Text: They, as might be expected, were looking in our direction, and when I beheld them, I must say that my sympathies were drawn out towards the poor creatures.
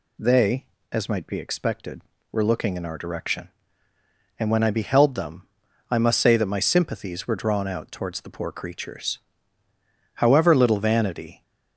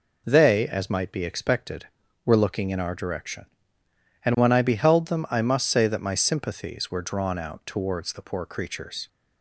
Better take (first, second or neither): second